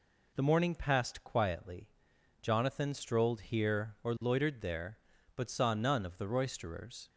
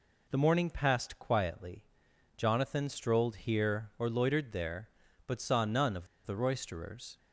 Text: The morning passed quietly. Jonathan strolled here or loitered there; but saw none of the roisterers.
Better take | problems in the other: first | pauses between "of" and "the"; slight; at 6.0 s; 0.19 s long

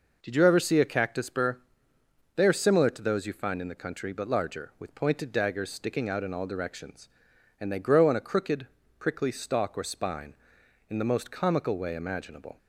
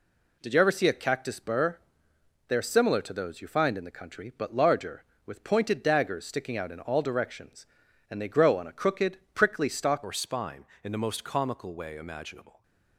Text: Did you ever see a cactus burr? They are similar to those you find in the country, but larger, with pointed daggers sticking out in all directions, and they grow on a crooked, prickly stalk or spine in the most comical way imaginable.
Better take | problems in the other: first | changes voice at "or"; from 10.0 s on; 2.6 s long

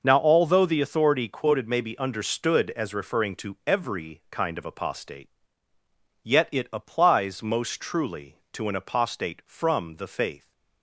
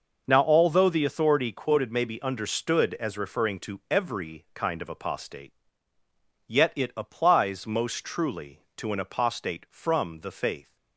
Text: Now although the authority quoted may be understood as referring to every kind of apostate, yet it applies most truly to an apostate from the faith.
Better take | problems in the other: neither | none

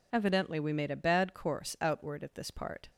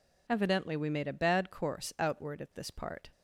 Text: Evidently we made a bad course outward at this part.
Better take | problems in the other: neither | none

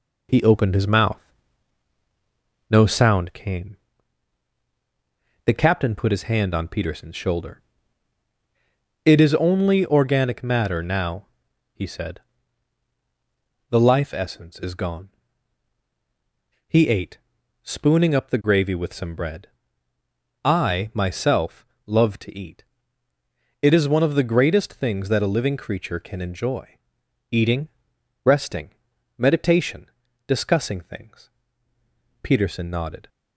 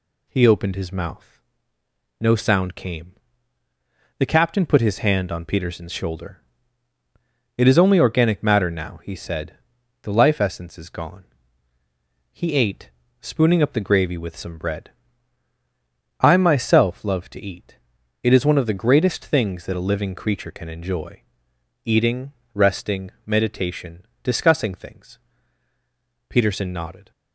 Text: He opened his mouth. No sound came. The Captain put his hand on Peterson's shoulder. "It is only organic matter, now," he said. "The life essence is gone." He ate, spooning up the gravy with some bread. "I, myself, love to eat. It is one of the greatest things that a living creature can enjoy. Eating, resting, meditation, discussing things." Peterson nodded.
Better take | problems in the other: second | gets quieter; throughout; 6 dB

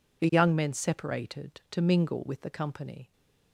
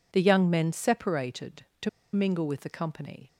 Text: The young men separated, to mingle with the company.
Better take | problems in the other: first | pauses between "to" and "mingle"; slight; at 1.8 s; 0.25 s long

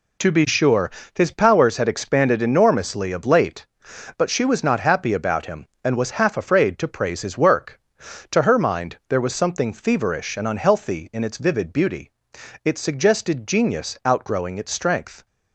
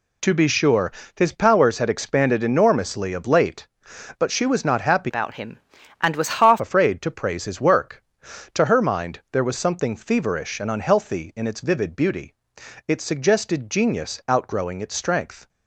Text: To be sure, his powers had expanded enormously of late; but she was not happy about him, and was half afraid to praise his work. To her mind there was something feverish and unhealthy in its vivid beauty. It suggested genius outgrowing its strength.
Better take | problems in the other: first | changes voice from "about" to "half"; from 5.0 to 6.6 s; 1.6 s long

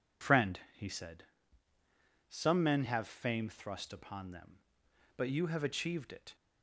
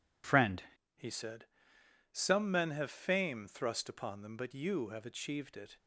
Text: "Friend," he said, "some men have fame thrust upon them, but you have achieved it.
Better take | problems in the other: first | changes voice at "he"; from 0.9 s on; 4.8 s long

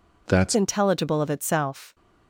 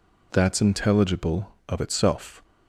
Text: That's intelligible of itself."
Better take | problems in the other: second | changes voice at "intelligible"; from 0.5 s on; 1.4 s long

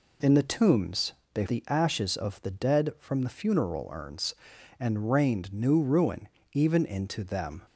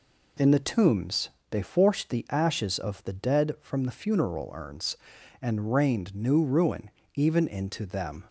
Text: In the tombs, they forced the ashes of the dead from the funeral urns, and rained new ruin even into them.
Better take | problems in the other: second | skips "forced"; at 1.4 s // pauses between "ruin" and "even"; slight; at 6.2 s; 0.24 s long; slight in the second

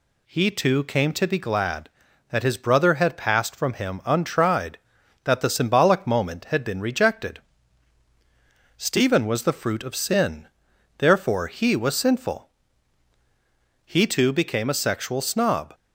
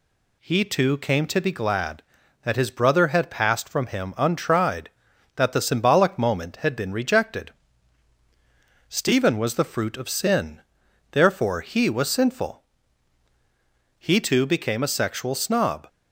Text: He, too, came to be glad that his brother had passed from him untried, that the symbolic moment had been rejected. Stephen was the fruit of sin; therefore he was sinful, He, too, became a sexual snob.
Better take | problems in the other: neither | none

